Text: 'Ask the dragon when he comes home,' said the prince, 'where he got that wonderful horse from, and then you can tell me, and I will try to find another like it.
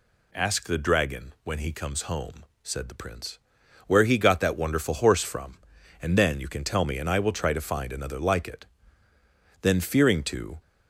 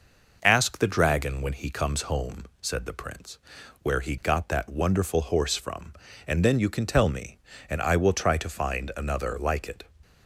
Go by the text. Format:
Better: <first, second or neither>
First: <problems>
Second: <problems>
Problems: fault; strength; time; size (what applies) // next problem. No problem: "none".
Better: second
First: goes on to say "Then fearing to"; noticeable; from 9.6 s on; 0.98 s long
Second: none